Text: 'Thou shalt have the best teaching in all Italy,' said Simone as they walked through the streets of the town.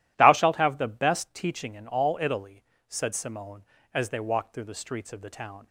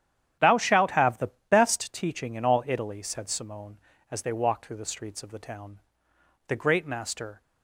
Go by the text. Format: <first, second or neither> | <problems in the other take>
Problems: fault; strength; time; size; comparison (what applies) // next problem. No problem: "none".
first | starts louder than the rest; strong; until 1.6 s; 10.5 dB // pauses between "the" and "best"; slight; at 1.2 s; 0.20 s long // goes on to say "The great master"; noticeable; from 6.4 s on; 0.94 s long